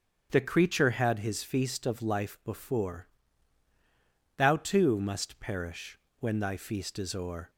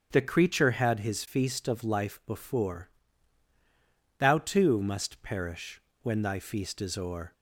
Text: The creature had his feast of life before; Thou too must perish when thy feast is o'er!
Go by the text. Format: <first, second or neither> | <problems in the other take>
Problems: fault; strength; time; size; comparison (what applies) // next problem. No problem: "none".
neither | starts louder than the rest; the same in both // pauses between "perish" and "when"; slight; the same in both